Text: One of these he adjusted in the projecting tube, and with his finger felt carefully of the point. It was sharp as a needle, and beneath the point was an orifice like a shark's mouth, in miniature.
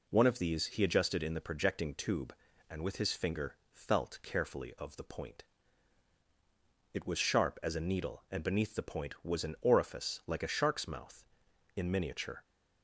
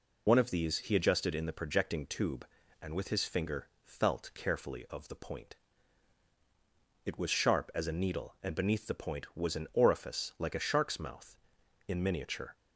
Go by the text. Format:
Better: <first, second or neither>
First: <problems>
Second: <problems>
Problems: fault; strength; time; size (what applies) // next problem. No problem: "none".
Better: first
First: pauses between "finger" and "felt"; slight; at 3.5 s; 0.16 s long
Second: loses the start of "One"; at 0.2 s; 60 ms // pauses between "finger" and "felt"; slight; at 3.6 s; 0.16 s long